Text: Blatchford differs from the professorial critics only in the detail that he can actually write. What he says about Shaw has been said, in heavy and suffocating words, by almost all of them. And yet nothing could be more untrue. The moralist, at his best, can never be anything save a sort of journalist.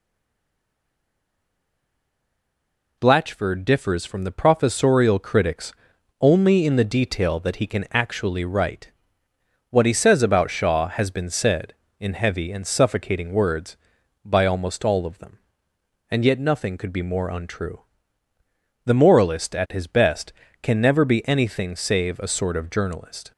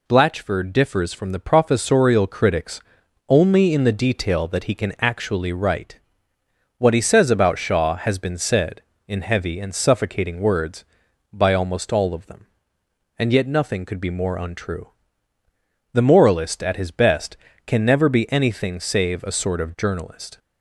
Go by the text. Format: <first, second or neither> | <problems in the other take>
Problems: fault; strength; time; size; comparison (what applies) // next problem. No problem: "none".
second | stays silent before the first word; strong; until 2.9 s; 2.9 s long // pauses between "critics" and "only"; noticeable; at 5.7 s; 0.48 s long; noticeable in the second